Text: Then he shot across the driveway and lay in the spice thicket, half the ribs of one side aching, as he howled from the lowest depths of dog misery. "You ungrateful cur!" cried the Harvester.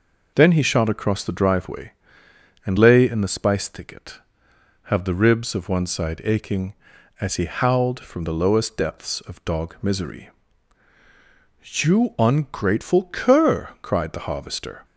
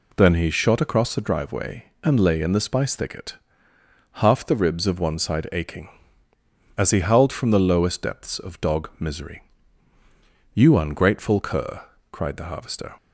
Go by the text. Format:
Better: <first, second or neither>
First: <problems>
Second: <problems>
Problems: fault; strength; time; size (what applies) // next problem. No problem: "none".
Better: second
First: says "have" for "half"; at 4.8 s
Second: none